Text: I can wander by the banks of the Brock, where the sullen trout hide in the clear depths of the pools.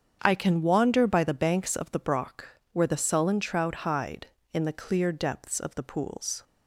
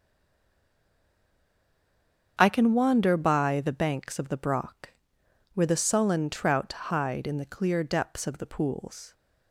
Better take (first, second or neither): first